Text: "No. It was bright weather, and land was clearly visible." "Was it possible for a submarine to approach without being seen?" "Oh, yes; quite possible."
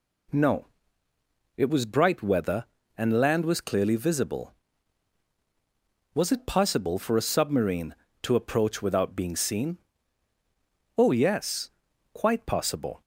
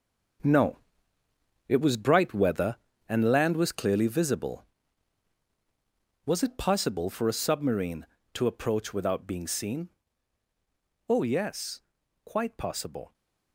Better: first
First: none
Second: gets quieter; strong; throughout; 10.5 dB

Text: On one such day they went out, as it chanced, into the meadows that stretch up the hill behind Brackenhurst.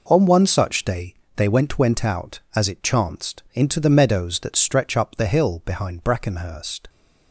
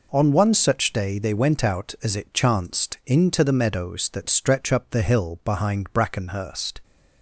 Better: second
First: pauses between "day" and "they"; slight; at 1.1 s; 0.20 s long // says "went" twice; at 1.7 s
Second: none

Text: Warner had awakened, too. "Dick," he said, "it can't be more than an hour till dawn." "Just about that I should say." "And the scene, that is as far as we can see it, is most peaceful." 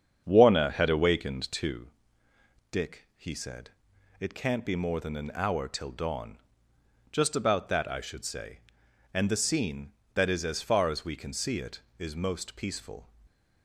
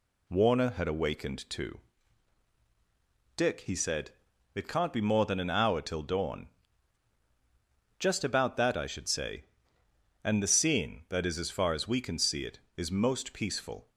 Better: second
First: starts louder than the rest; strong; until 1.8 s; 7.5 dB // stays silent after the last word; slight; from 13.0 s on; 0.6 s long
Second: none

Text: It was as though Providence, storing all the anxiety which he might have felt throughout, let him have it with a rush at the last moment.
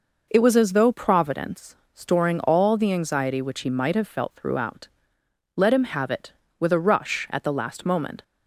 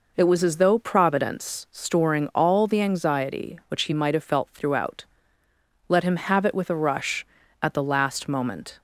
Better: neither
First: none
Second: none

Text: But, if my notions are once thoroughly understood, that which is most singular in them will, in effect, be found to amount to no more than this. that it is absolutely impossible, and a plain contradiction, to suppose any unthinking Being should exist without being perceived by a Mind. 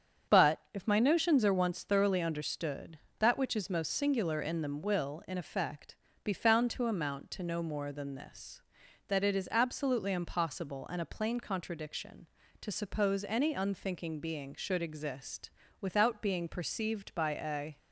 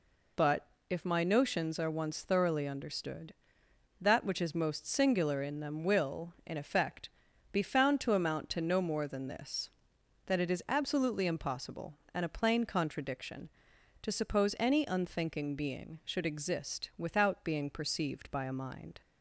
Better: second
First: starts louder than the rest; strong; until 1.4 s; 7.5 dB // pauses between "exist" and "without"; slight; at 15.4 s; 0.32 s long // stops before "Mind"; at 17.7 s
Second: none

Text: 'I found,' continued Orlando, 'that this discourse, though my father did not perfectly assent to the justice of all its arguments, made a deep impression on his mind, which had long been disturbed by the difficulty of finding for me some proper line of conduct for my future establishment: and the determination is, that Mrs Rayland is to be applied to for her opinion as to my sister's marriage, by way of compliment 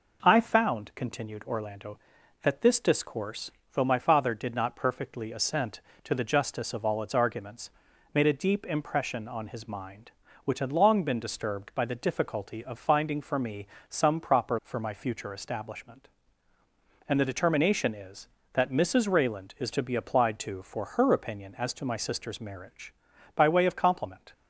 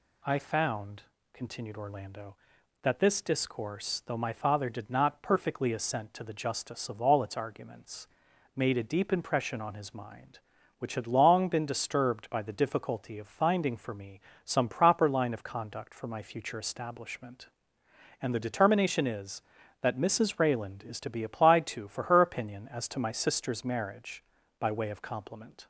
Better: second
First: pauses between "me" and "some"; slight; at 13.6 s; 0.24 s long // skips "line of conduct"; at 14.6 s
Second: pauses between "me" and "some"; slight; at 14.1 s; 0.24 s long

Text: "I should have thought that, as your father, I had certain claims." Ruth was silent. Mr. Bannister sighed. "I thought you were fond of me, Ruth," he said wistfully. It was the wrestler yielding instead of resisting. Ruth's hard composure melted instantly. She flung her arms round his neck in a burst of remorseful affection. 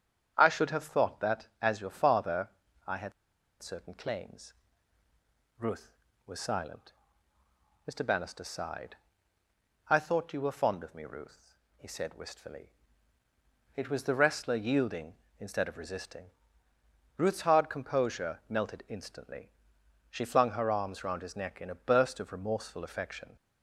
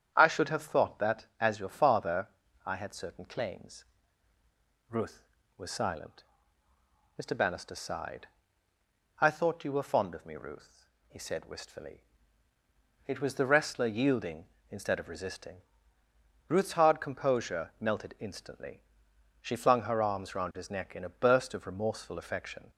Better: second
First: starts louder than the rest; strong; until 1.3 s; 8.5 dB // pauses between "had" and "certain"; noticeable; at 3.1 s; 0.49 s long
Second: starts louder than the rest; strong; until 1.1 s; 8.5 dB

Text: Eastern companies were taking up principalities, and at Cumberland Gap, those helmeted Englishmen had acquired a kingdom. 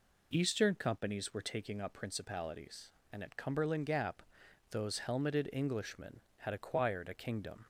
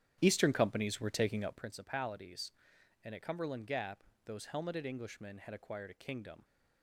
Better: first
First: none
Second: starts louder than the rest; strong; until 1.7 s; 10 dB

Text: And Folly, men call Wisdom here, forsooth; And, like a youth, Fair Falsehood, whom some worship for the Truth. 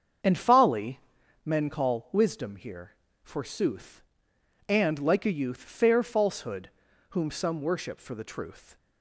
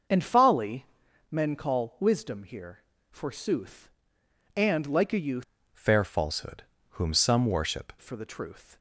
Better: first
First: starts louder than the rest; until 1.7 s; 7 dB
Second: starts louder than the rest; noticeable; until 1.5 s; 6 dB // changes voice from "Fair" to "worship"; from 5.7 to 7.9 s; 2.2 s long

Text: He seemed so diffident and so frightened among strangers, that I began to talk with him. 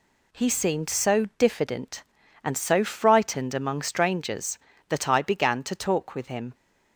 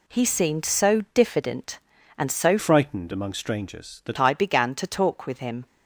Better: first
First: none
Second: changes voice from "frightened" to "that"; from 2.5 to 4.1 s; 1.6 s long

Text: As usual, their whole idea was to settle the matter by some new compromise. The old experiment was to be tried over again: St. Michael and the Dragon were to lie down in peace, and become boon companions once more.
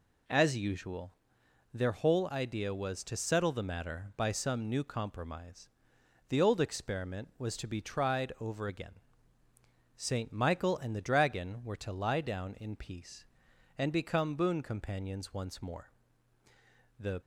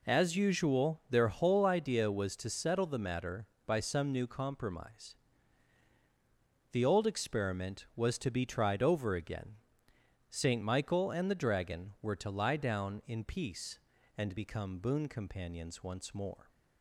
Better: second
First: goes on to say "The"; slight; from 16.9 s on; 0.22 s long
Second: none

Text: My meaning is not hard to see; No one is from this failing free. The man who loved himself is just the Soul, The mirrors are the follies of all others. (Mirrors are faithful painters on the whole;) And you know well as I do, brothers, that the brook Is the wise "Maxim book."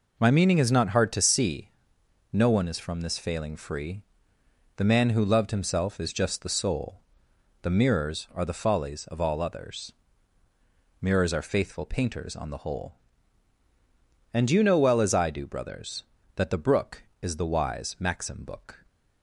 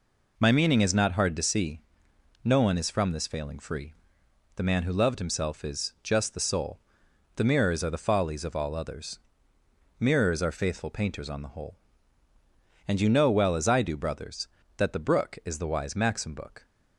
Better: neither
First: none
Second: none

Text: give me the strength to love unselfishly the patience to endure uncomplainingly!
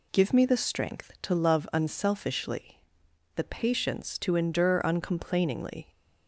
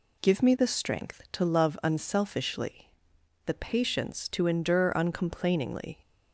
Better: neither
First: pauses between "unselfishly" and "the"; noticeable; at 2.7 s; 0.56 s long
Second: pauses between "unselfishly" and "the"; noticeable; at 2.8 s; 0.56 s long

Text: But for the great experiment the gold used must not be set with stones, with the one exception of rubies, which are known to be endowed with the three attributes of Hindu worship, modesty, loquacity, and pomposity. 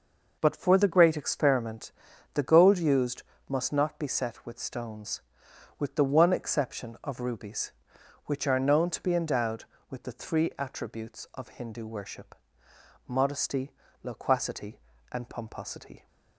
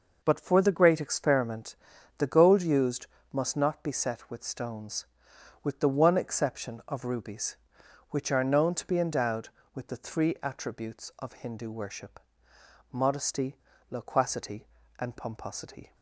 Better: neither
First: pauses between "experiment" and "the"; at 1.9 s; 0.44 s long // pauses between "used" and "must"; slight; at 3.2 s; 0.26 s long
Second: pauses between "experiment" and "the"; at 1.7 s; 0.44 s long // pauses between "used" and "must"; slight; at 3.0 s; 0.26 s long

